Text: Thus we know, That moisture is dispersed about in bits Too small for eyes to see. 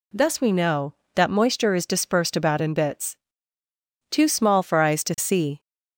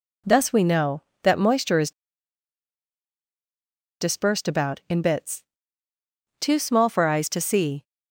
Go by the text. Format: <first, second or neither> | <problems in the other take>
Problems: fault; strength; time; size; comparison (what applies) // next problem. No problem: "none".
first | pauses between "is" and "dispersed"; strong; at 1.9 s; 2.1 s long // pauses between "bits" and "Too"; noticeable; at 5.4 s; 0.96 s long; noticeable in the first